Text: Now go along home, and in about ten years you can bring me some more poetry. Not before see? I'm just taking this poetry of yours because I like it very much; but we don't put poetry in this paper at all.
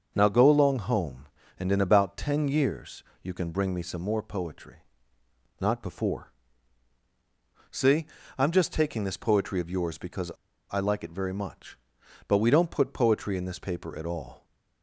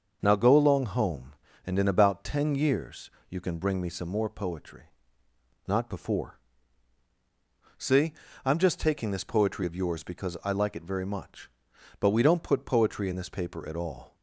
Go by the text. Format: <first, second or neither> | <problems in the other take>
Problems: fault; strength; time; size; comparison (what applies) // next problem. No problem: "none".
second | starts louder than the rest; until 1.1 s; 6.5 dB; also in the second // pauses between "years" and "you"; slight; at 3.0 s; 0.20 s long; slight in the second // pauses between "before" and "see"; strong; at 6.2 s; 1.4 s long; strong in the second // pauses between "because" and "I"; at 10.3 s; 0.39 s long